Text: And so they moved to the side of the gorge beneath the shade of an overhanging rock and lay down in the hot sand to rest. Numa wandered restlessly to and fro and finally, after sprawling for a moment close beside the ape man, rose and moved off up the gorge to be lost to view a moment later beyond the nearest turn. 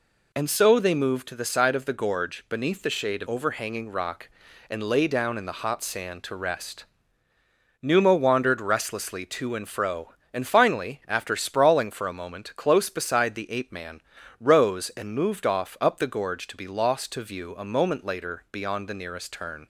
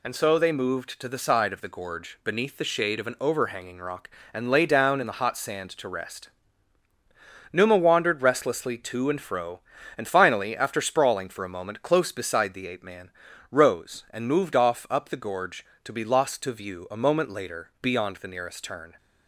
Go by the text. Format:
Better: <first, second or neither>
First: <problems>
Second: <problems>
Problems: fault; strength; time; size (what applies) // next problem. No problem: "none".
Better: second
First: skips "an"; at 3.2 s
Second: none